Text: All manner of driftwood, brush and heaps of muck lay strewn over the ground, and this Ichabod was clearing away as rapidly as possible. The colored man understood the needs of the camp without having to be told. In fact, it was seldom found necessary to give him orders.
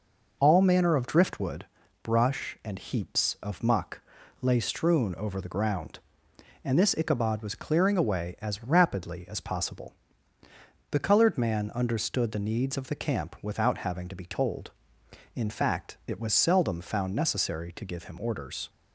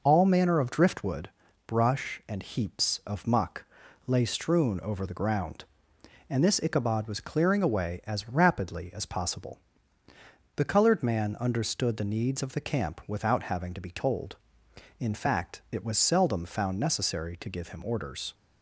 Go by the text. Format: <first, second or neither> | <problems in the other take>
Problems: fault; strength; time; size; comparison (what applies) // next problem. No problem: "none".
neither | pauses between "muck" and "lay"; the same in both